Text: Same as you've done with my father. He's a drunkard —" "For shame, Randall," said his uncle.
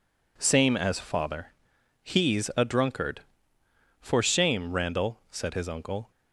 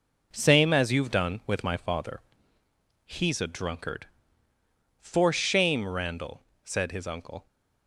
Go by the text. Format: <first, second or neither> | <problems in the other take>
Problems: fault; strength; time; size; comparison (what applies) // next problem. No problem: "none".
second | skips "you've done with my"; at 0.9 s